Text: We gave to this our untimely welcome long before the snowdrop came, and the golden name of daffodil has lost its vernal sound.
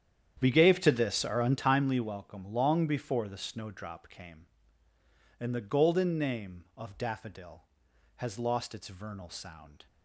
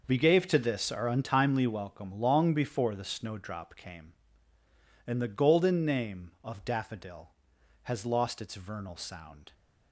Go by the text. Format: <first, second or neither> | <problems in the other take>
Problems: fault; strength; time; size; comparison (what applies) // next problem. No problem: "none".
second | starts louder than the rest; strong; until 1.9 s; 9.5 dB